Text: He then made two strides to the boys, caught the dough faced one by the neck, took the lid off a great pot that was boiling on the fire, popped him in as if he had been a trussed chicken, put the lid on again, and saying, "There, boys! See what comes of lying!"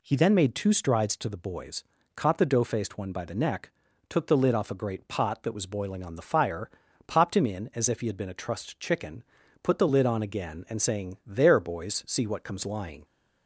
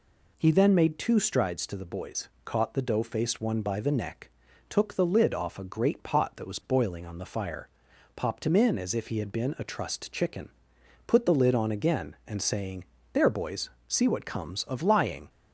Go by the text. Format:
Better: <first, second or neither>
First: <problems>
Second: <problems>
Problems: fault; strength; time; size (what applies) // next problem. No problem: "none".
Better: second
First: skips "of"; at 12.6 s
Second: none